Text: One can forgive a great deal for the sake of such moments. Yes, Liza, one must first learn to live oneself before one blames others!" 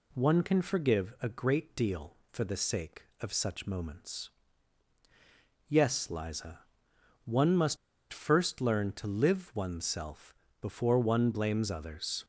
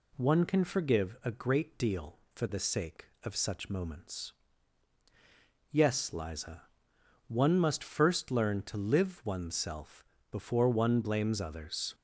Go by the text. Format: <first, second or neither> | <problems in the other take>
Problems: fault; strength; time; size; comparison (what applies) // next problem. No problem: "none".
second | pauses between "must" and "first"; slight; at 7.7 s; 0.35 s long // pauses between "oneself" and "before"; slight; at 10.3 s; 0.26 s long; slight in the second